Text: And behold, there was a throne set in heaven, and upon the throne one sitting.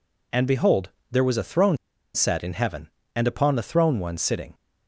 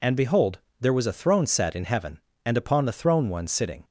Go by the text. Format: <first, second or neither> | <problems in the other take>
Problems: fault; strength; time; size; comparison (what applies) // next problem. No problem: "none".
second | pauses between "throne" and "set"; at 1.7 s; 0.39 s long